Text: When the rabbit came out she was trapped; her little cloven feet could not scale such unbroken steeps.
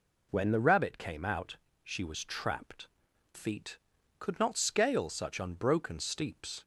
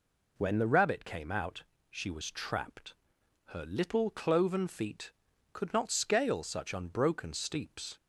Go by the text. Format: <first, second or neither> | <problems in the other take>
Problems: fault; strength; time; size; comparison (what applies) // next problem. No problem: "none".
second | pauses between "out" and "she"; slight; at 1.5 s; 0.28 s long; slight in the second // skips "her little cloven"; at 3.1 s